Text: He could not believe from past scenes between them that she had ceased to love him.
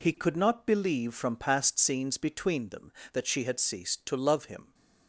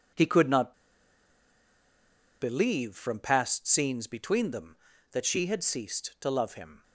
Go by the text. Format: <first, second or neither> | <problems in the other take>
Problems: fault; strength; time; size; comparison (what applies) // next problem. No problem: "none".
first | pauses between "not" and "believe"; strong; at 0.7 s; 1.6 s long